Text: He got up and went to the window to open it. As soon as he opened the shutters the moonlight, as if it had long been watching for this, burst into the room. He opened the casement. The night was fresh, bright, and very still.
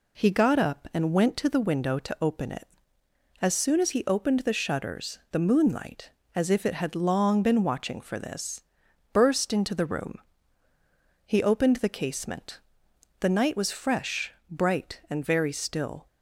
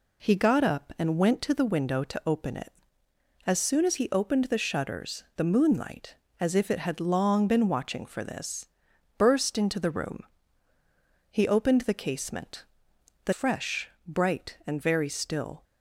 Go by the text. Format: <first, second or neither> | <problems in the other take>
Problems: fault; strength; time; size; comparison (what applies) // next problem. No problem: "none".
first | skips "night was"; at 13.3 s